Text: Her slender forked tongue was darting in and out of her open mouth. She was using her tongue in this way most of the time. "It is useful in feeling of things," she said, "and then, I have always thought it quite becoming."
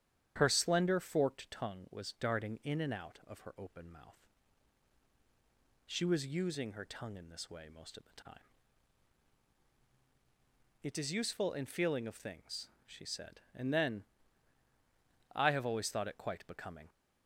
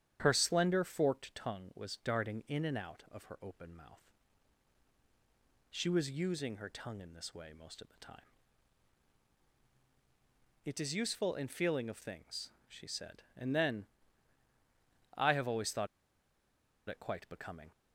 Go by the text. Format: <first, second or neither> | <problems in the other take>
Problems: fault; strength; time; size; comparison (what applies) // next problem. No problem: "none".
first | starts louder than the rest; strong; until 1.2 s; 9.5 dB; strong in the first // pauses between "thought" and "it"; at 15.8 s; 1.0 s long